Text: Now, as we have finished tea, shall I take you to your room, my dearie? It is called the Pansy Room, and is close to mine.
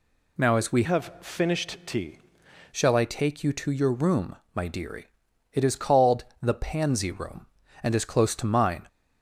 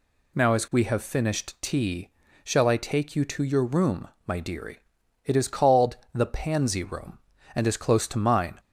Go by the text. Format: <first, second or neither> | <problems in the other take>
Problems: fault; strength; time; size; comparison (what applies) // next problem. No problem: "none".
second | changes voice from "have" to "tea"; from 0.8 to 2.1 s; 1.3 s long // pauses between "called" and "the"; slight; at 6.2 s; 0.16 s long; slight in the second